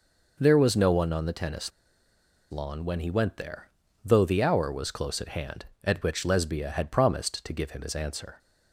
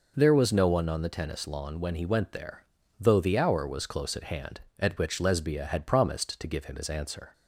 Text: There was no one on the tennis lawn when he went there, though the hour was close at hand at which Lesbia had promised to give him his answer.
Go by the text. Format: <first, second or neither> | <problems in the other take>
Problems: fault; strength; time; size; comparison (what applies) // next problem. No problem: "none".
second | pauses between "tennis" and "lawn"; noticeable; at 1.7 s; 0.81 s long